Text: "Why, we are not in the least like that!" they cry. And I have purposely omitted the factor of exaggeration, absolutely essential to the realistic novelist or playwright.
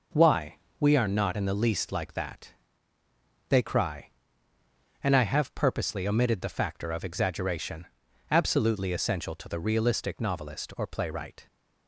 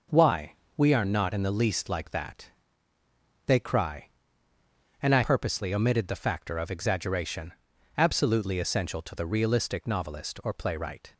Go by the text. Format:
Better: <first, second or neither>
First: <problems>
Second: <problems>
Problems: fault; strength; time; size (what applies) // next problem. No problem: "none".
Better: first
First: none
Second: skips "have"; at 5.2 s